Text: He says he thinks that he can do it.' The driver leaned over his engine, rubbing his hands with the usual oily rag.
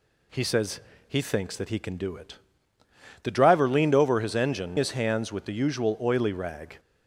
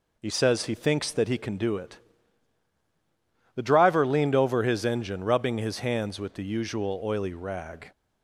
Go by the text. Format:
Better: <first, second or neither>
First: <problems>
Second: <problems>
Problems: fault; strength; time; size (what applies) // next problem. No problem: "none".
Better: second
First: pauses between "says" and "he"; slight; at 0.8 s; 0.26 s long // skips "rubbing"; at 4.7 s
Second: none